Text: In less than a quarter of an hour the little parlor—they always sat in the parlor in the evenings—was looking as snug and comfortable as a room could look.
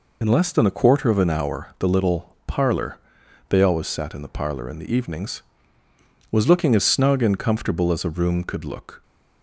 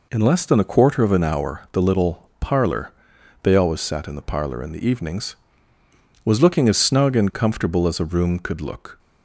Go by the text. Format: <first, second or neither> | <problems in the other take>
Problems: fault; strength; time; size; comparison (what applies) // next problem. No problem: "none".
second | loses the start of "In"; at 0.2 s; 40 ms